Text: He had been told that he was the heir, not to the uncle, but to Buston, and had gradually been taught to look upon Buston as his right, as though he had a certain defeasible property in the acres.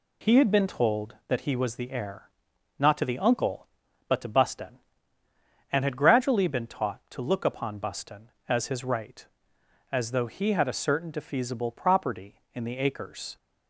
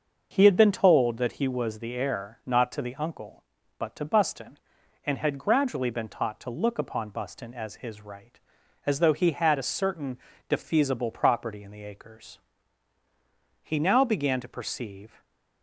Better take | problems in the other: first | starts louder than the rest; until 1.3 s; 6 dB // pauses between "certain" and "defeasible"; slight; at 10.1 s; 0.30 s long // goes on to say "He now began to perceive"; from 13.6 s on; 1.5 s long // stays silent after the last word; slight; from 15.0 s on; 0.6 s long

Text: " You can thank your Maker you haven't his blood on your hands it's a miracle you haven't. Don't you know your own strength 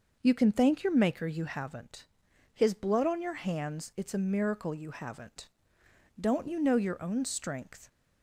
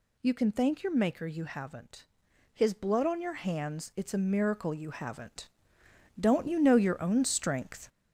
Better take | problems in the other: first | gets louder; throughout; 6.5 dB // pauses between "haven't" and "his"; noticeable; at 2.0 s; 0.48 s long; noticeable in the first

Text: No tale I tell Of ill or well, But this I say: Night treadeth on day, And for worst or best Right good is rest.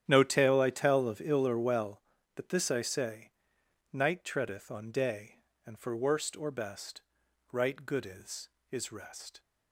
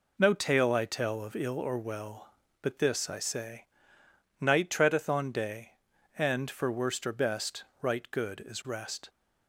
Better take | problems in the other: second | starts louder than the rest; strong; until 1.0 s; 10 dB // pauses between "best" and "Right"; noticeable; at 7.0 s; 0.48 s long; slight in the second // says "is" twice; at 8.7 s

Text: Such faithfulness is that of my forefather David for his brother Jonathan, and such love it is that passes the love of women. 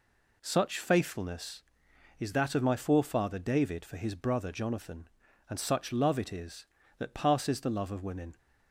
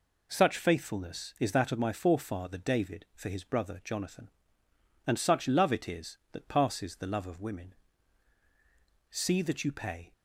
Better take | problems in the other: first | goes on to say "See that you pay"; noticeable; from 9.1 s on; 1.0 s long

